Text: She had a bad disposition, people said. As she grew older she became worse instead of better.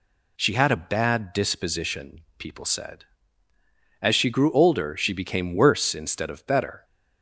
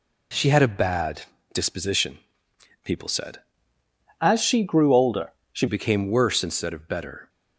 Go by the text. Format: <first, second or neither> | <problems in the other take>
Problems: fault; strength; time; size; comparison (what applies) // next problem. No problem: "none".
first | pauses between "bad" and "disposition"; slight; at 1.2 s; 0.30 s long // changes voice from "As" to "she"; from 4.2 to 5.6 s; 1.4 s long // pauses between "older" and "she"; slight; at 5.3 s; 0.18 s long